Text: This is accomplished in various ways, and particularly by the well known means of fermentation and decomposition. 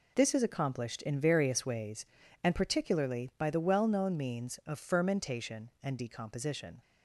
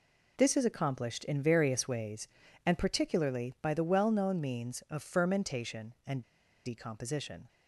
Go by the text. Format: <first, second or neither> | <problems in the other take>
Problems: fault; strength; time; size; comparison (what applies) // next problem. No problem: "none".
first | pauses between "and" and "decomposition"; at 6.2 s; 0.43 s long